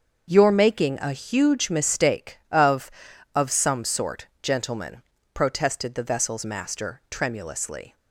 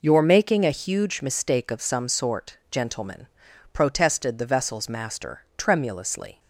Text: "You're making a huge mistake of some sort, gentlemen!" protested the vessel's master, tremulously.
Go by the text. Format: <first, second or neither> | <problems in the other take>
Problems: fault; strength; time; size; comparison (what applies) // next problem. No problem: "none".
second | starts louder than the rest; until 1.3 s; 6.5 dB // says "of" twice; at 3.3 s